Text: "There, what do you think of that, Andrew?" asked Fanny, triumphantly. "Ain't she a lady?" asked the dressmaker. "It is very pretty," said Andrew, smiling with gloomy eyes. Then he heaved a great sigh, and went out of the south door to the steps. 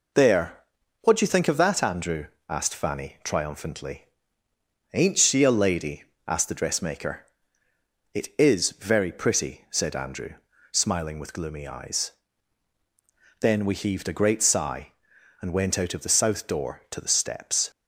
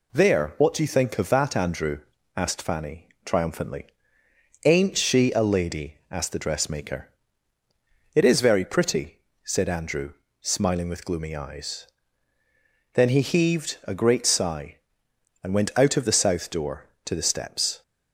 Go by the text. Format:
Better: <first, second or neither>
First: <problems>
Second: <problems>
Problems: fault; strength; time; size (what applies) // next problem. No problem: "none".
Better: second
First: says "we" for "he"; at 13.6 s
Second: none